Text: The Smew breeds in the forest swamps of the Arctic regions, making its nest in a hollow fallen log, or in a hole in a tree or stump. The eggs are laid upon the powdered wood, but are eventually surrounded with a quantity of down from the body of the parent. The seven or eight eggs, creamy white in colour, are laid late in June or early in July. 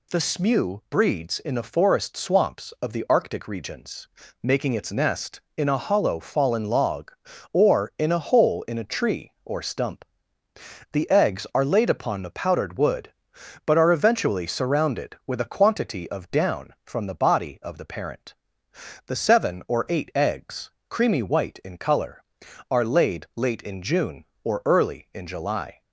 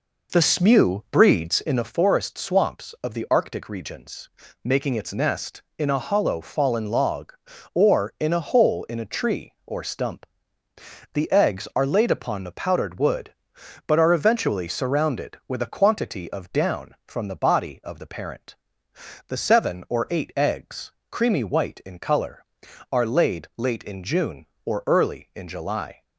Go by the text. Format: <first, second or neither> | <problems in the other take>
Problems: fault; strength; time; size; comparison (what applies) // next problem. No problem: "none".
first | starts louder than the rest; noticeable; until 1.9 s; 4.5 dB